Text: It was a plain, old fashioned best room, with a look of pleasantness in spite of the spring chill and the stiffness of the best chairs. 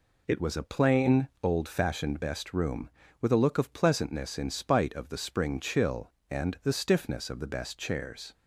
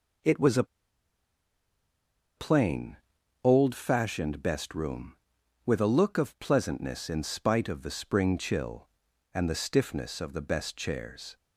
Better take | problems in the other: first | pauses between "a" and "plain"; strong; at 0.6 s; 1.7 s long

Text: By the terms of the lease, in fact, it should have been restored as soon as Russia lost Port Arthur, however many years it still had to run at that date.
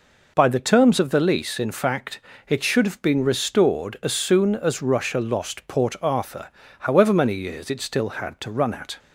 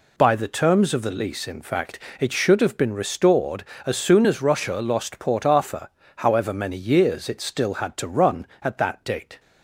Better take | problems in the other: second | stops before "that date"; at 8.9 s

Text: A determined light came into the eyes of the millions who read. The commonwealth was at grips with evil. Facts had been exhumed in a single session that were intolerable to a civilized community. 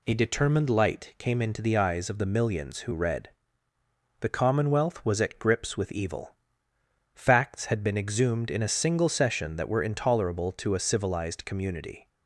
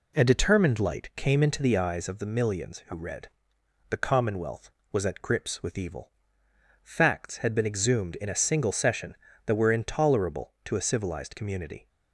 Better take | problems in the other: neither | none

